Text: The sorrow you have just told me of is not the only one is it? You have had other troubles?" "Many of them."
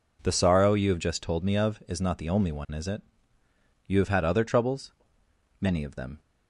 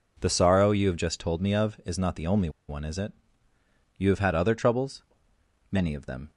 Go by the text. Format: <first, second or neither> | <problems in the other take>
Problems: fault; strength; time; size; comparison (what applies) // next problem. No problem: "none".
first | pauses between "only" and "one"; slight; at 2.4 s; 0.18 s long